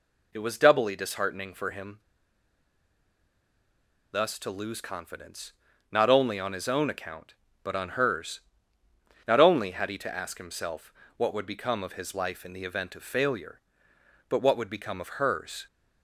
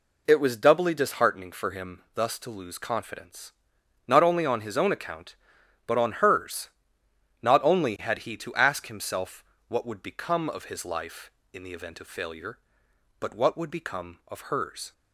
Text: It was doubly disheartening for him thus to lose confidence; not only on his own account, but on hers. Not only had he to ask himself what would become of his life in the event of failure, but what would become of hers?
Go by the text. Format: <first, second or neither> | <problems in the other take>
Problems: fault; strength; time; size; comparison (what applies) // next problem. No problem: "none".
second | pauses between "him" and "thus"; strong; at 1.9 s; 2.1 s long // pauses between "himself" and "what"; slight; at 10.9 s; 0.24 s long; slight in the second